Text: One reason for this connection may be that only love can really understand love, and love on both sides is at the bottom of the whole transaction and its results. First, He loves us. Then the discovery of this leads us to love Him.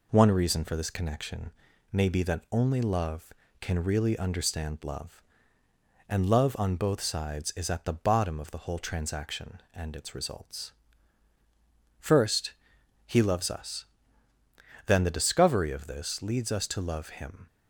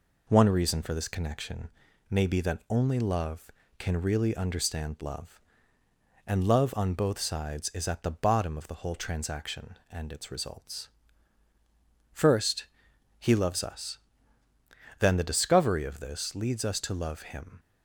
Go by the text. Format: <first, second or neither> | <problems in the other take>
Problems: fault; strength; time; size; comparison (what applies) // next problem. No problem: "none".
neither | pauses between "connection" and "may"; the same in both